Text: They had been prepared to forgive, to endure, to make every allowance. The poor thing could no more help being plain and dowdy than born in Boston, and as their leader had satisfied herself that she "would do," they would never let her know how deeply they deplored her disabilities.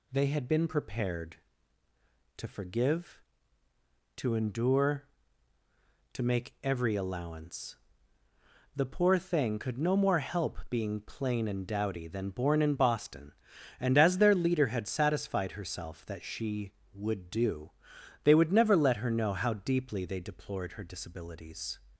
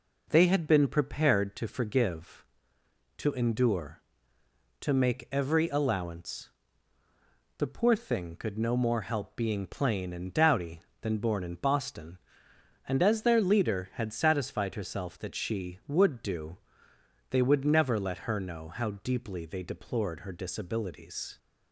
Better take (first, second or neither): neither